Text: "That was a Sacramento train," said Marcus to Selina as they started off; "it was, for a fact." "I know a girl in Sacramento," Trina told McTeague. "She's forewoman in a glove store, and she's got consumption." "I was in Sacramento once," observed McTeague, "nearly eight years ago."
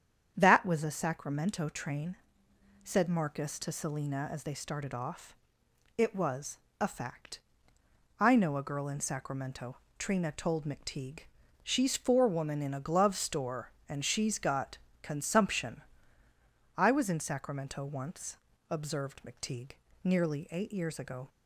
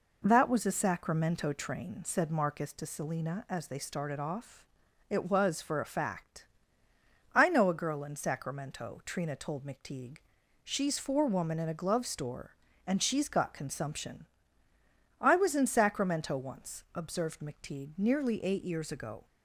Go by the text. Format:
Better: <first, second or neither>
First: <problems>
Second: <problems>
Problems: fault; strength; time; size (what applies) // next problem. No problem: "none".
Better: second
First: starts louder than the rest; strong; until 1.3 s; 8.5 dB // skips "for"; at 6.6 s // pauses between "got" and "consumption"; slight; at 14.7 s; 0.26 s long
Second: none